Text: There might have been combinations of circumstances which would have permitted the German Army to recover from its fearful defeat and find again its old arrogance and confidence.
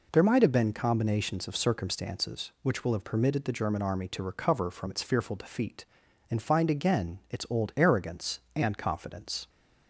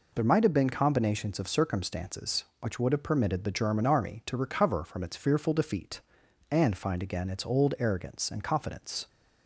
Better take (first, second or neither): second